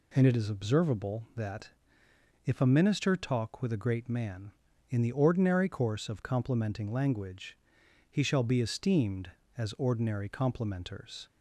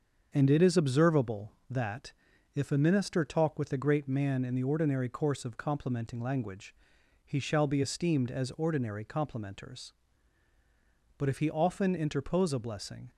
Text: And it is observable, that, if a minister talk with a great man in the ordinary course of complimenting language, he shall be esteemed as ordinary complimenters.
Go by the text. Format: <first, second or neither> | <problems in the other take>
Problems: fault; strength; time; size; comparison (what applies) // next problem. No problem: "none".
first | starts louder than the rest; until 1.3 s; 7 dB // goes on to say "But if he often interpose a blessing"; strong; from 11.1 s on; 1.9 s long